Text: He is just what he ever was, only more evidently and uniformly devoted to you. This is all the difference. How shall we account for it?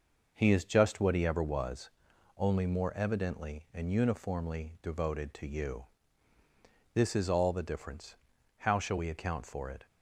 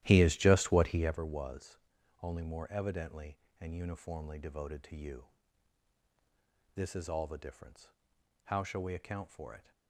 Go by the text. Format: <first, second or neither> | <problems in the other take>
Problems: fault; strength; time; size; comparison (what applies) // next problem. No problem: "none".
first | starts louder than the rest; strong; until 1.2 s; 13.5 dB